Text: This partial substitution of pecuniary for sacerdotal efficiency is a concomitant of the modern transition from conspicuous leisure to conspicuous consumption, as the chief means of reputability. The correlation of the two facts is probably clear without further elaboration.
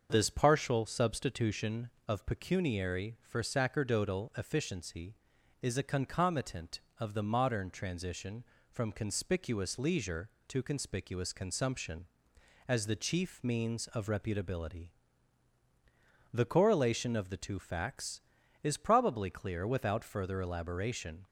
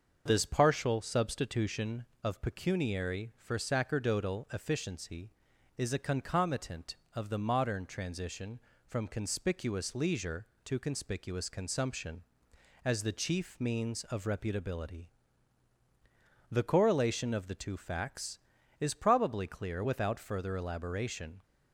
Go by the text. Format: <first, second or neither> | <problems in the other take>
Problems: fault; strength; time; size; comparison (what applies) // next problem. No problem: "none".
neither | starts louder than the rest; the same in both